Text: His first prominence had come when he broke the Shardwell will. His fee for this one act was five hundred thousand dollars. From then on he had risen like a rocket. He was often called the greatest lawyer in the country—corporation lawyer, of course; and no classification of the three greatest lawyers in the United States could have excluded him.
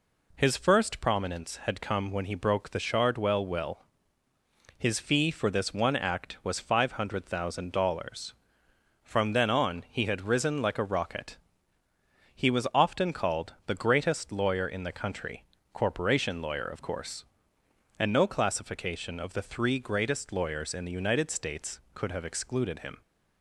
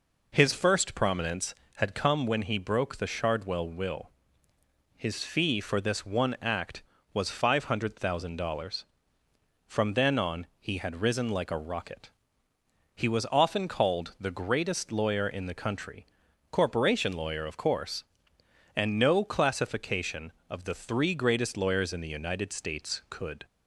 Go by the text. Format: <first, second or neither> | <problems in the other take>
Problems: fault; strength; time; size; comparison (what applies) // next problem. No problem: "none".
first | stops before "have excluded him"; at 23.4 s